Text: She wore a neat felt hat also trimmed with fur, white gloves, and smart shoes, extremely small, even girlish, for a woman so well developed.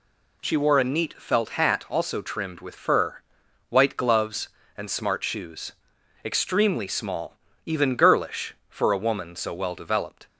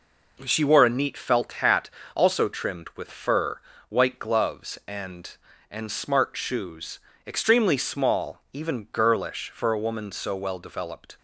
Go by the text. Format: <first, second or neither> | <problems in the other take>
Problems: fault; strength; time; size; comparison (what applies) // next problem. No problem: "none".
first | pauses between "hat" and "also"; slight; at 1.8 s; 0.24 s long // says "and" twice; at 5.7 s